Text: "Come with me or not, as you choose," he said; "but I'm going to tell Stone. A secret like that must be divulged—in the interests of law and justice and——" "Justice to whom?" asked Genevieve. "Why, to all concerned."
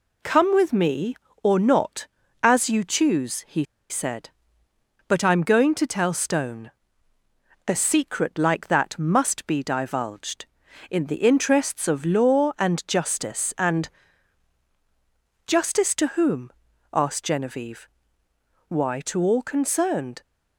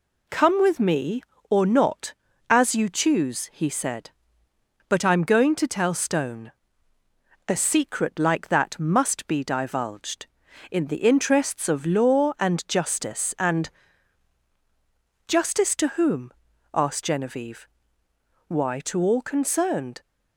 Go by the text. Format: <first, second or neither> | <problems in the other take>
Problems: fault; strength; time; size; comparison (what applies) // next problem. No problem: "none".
second | pauses between "he" and "said"; slight; at 3.6 s; 0.25 s long